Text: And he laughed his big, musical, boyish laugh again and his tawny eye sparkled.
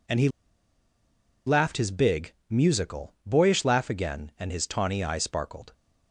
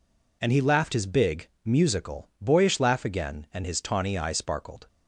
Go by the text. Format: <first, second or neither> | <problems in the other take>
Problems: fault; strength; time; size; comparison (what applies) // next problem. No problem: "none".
second | pauses between "he" and "laughed"; at 0.2 s; 1.1 s long